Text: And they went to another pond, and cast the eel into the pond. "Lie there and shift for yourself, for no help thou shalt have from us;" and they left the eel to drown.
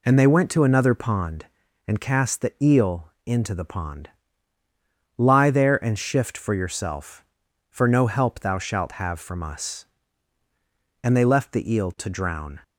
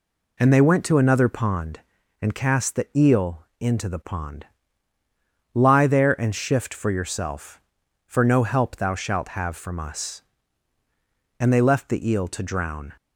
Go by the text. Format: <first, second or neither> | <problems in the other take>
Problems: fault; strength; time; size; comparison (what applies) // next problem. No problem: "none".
neither | none